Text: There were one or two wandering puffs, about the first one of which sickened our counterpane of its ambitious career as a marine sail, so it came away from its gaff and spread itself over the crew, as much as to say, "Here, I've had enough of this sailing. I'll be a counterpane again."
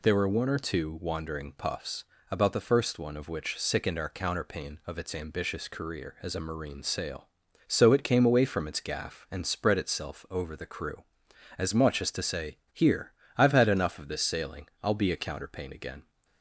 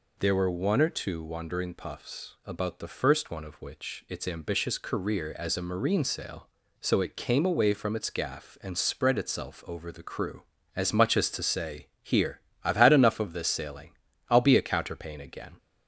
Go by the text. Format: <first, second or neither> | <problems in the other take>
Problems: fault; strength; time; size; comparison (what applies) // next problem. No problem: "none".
first | skips "sickened our counterpane of"; at 4.0 s